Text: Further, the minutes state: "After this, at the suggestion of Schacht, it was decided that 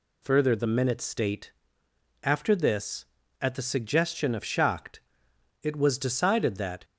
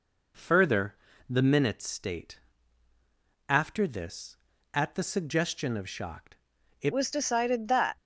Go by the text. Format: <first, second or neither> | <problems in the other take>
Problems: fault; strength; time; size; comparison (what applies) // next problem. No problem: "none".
first | changes voice at "was"; from 6.9 s on; 1.0 s long